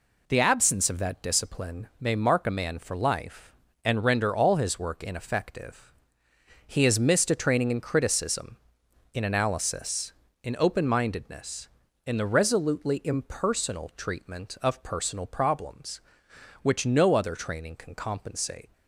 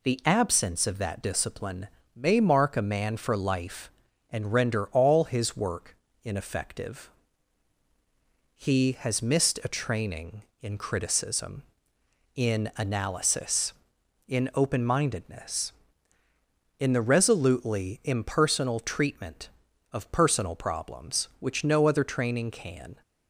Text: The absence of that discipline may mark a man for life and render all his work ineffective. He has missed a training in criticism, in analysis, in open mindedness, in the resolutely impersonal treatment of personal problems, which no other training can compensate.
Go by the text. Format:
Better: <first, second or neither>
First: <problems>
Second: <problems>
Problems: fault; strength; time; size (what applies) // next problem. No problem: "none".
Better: first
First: none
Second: pauses between "discipline" and "may"; slight; at 1.8 s; 0.28 s long // pauses between "work" and "ineffective"; slight; at 5.9 s; 0.28 s long // stops before "compensate"; at 23.0 s